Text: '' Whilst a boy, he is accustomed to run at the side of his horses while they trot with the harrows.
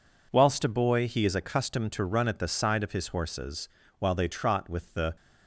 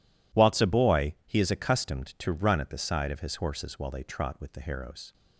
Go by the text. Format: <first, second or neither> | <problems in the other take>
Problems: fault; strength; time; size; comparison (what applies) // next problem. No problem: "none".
second | pauses between "horses" and "while"; slight; at 3.6 s; 0.30 s long // stops before "harrows"; at 5.1 s